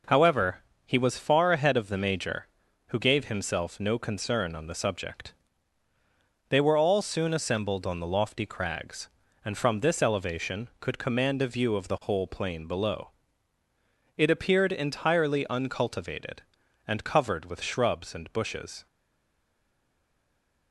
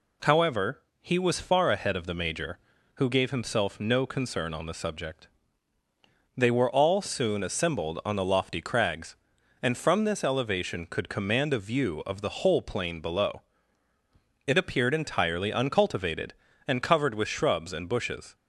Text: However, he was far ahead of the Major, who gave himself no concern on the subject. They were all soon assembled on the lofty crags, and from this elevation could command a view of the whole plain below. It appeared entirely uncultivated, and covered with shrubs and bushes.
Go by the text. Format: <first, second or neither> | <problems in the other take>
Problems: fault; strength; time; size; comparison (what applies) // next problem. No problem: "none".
second | stays silent after the last word; noticeable; from 18.8 s on; 1.9 s long